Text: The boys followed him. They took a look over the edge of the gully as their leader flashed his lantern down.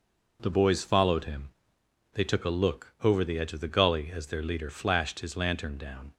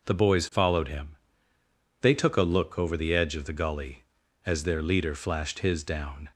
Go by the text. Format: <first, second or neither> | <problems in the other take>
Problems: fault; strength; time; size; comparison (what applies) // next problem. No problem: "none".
first | skips "lantern"; at 5.8 s